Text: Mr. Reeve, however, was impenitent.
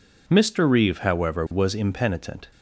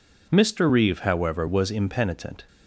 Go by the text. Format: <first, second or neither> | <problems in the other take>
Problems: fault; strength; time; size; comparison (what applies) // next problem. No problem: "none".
neither | none